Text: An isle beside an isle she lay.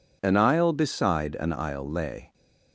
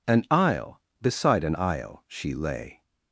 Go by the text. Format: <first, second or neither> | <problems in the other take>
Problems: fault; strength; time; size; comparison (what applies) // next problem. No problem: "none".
second | skips "she"; at 1.8 s